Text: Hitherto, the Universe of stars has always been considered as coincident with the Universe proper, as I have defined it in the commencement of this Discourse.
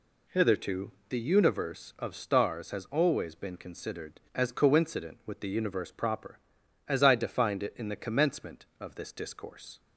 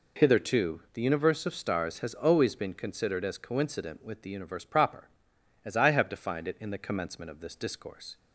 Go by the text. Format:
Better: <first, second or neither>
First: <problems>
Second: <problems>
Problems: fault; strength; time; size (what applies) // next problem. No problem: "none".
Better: second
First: skips "have"; at 7.1 s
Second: none